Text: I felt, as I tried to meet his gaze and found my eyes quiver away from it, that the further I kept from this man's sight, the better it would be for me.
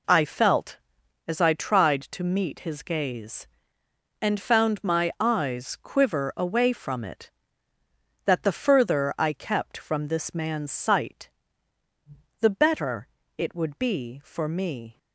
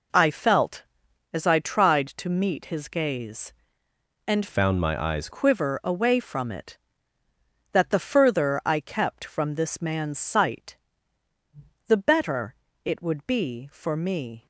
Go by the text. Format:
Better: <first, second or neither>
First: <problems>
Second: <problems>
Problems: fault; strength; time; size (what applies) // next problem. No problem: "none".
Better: first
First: pauses between "better" and "it"; slight; at 13.0 s; 0.28 s long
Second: changes voice from "found" to "eyes"; from 4.4 to 5.2 s; 0.8 s long // pauses between "better" and "it"; slight; at 12.5 s; 0.28 s long